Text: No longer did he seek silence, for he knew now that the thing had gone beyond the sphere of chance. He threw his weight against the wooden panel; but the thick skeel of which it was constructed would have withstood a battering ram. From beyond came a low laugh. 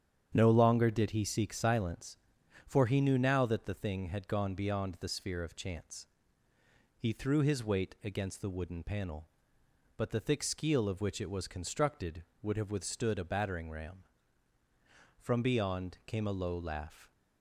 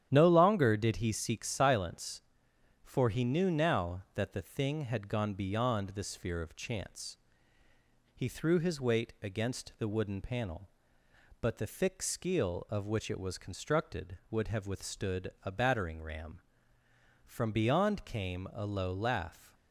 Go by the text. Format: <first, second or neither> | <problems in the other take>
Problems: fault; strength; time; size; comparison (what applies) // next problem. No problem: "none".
neither | starts louder than the rest; strong; the same in both